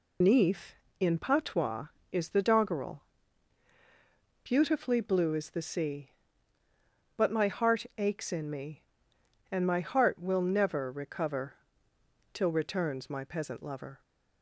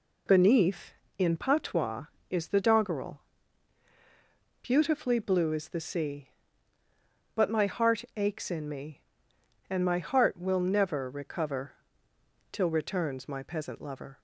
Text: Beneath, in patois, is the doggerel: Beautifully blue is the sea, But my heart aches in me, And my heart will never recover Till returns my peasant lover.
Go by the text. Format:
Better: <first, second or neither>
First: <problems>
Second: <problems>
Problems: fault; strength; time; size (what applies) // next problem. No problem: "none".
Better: second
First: loses the start of "Beneath"; at 0.2 s; 125 ms // pauses between "recover" and "Till"; noticeable; at 11.5 s; 0.76 s long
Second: pauses between "recover" and "Till"; noticeable; at 11.7 s; 0.76 s long